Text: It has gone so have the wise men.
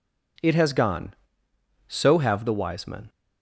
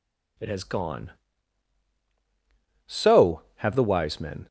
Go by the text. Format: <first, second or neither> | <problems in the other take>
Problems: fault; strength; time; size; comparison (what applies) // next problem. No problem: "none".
neither | none